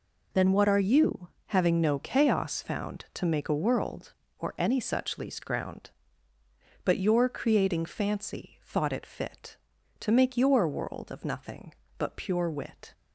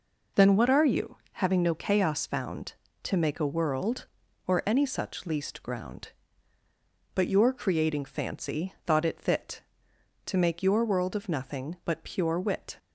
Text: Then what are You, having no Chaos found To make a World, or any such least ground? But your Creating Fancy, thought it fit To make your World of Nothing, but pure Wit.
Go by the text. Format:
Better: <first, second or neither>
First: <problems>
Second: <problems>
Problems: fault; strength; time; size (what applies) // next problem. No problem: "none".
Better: neither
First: none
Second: none